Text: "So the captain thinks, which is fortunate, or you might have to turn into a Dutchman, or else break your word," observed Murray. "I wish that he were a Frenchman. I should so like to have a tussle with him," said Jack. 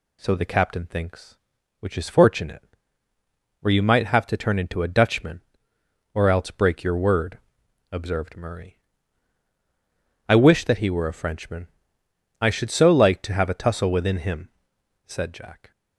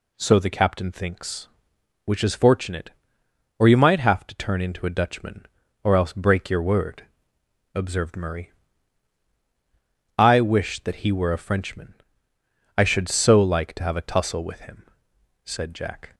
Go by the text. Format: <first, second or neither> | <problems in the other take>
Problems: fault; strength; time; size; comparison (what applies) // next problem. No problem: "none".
second | says "within" for "with"; at 13.9 s